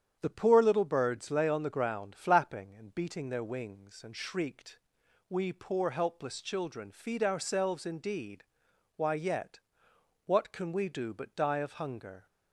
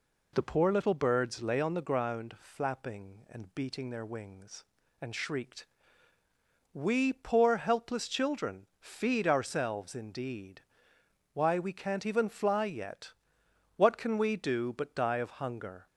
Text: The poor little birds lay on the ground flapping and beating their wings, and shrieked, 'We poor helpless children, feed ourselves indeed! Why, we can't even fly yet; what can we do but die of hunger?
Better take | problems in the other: second | starts louder than the rest; strong; until 1.2 s; 8.5 dB // skips "we can't even fly"; at 9.1 s

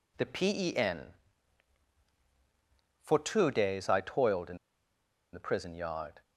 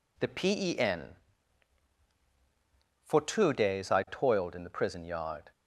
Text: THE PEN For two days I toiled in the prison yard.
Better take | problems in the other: second | pauses between "in" and "the"; noticeable; at 4.5 s; 0.77 s long

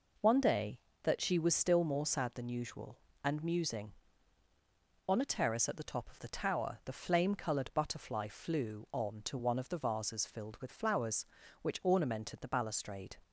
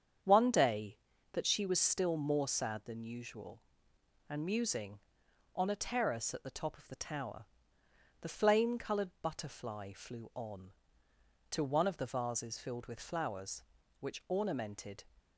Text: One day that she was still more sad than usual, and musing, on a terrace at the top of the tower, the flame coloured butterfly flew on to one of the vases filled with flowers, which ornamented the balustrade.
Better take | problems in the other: first | starts louder than the rest; strong; until 1.5 s; 8 dB // stops before "the balustrade"; at 15.1 s

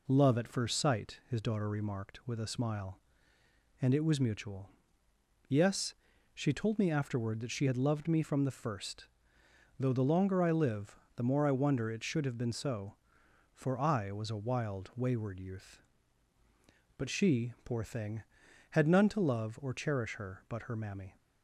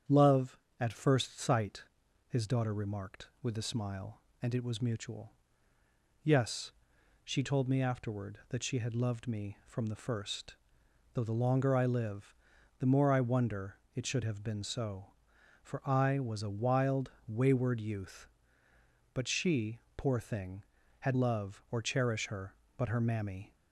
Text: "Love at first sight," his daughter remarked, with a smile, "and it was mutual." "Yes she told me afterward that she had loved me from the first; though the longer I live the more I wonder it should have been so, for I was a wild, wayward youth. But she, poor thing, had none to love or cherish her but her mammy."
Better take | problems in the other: first | starts louder than the rest; strong; until 1.3 s; 8.5 dB // pauses between "Yes" and "she"; noticeable; at 6.6 s; 0.54 s long; also in the first // pauses between "live" and "the"; at 12.3 s; 0.42 s long; slight in the first // pauses between "wonder" and "it"; slight; at 13.7 s; 0.16 s long // skips "none to"; at 21.1 s

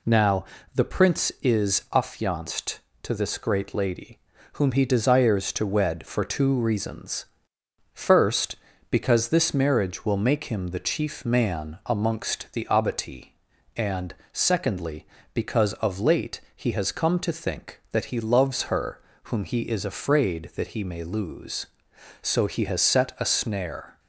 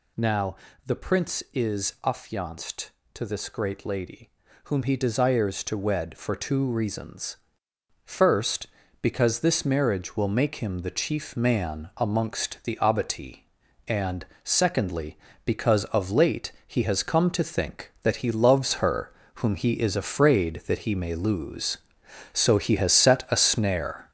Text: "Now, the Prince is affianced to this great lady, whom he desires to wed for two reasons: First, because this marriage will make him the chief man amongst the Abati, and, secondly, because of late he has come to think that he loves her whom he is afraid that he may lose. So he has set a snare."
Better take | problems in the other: first | gets louder; noticeable; throughout; 6 dB // pauses between "late" and "he"; slight; at 16.5 s; 0.16 s long; slight in the first // pauses between "her" and "whom"; slight; at 19.1 s; 0.24 s long; slight in the first

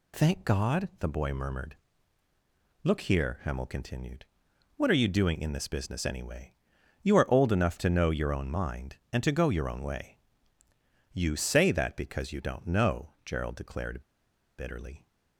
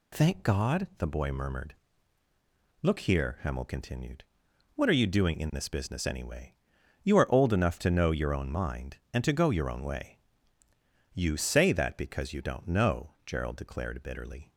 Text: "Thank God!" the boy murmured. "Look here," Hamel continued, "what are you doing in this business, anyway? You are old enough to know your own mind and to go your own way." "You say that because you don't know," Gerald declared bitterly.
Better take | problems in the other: second | pauses between "declared" and "bitterly"; noticeable; at 14.0 s; 0.57 s long

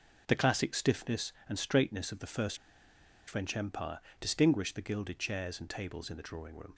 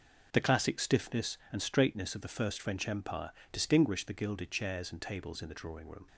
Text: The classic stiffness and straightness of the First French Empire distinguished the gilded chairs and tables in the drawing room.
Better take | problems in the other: second | pauses between "First" and "French"; noticeable; at 2.5 s; 0.71 s long // pauses between "Empire" and "distinguished"; slight; at 3.9 s; 0.22 s long; slight in the second

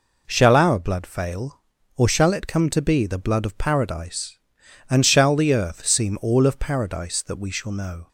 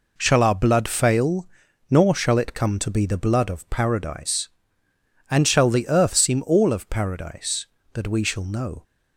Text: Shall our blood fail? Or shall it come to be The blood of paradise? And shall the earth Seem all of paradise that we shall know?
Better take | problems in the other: first | says "Nor" for "Or"; at 1.8 s

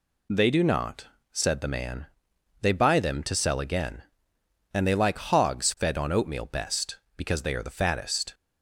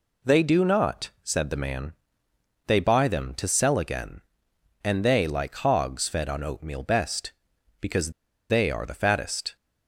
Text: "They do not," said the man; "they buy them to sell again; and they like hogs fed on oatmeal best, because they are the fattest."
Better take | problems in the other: first | pauses between "because" and "they"; at 8.1 s; 0.39 s long

